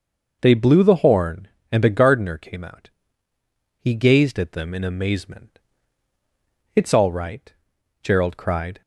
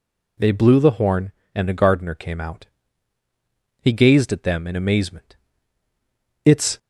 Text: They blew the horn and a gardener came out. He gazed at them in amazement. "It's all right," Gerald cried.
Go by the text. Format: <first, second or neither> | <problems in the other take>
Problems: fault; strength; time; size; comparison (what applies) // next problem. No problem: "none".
first | stops before "all right Gerald cried"; at 6.7 s